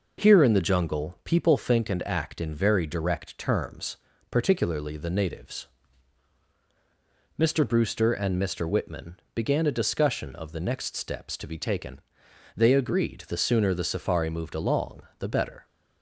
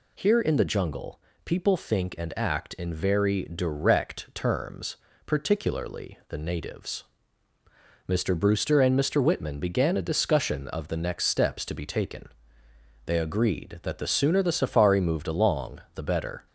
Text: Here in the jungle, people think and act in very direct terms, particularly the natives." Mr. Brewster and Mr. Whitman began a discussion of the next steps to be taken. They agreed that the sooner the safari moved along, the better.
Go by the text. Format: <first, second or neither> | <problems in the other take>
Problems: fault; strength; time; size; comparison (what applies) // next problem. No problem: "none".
second | pauses between "Whitman" and "began"; slight; at 9.1 s; 0.16 s long // skips "that"; at 13.2 s